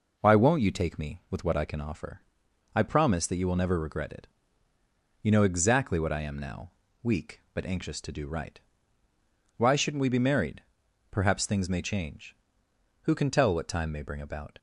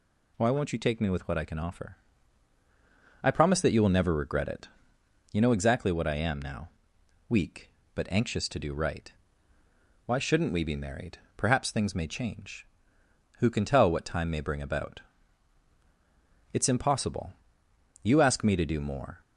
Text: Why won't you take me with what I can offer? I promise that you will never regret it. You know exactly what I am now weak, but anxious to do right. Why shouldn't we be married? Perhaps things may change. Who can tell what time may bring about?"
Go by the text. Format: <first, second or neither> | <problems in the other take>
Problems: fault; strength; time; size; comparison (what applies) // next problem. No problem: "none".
first | pauses between "now" and "weak"; noticeable; at 6.6 s; 0.58 s long; slight in the first // goes on to say "It's impossible You ask me to do more"; strong; from 16.5 s on; 2.6 s long